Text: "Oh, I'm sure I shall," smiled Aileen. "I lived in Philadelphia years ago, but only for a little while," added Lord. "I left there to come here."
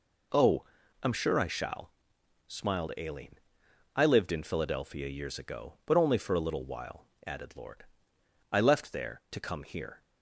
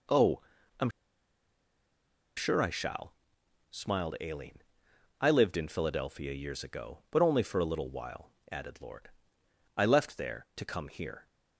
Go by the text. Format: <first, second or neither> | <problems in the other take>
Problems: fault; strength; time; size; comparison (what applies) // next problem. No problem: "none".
first | pauses between "I'm" and "sure"; strong; at 0.8 s; 1.4 s long